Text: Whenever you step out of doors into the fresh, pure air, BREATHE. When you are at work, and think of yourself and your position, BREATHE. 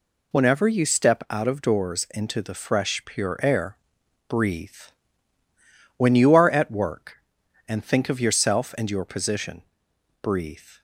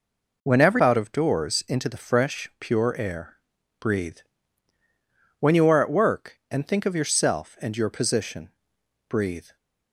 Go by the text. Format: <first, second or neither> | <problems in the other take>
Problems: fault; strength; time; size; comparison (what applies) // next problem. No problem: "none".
first | skips "you step"; at 0.7 s